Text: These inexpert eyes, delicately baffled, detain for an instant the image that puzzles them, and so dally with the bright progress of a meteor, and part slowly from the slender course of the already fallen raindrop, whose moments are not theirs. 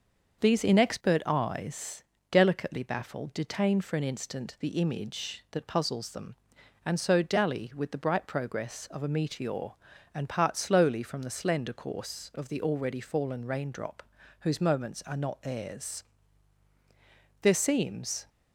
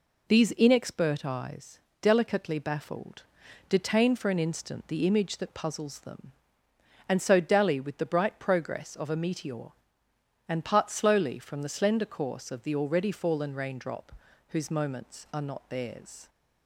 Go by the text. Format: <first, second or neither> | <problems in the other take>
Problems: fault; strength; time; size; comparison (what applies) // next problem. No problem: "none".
second | starts louder than the rest; until 1.4 s; 6 dB // goes on to say "There seems"; noticeable; from 17.4 s on; 0.88 s long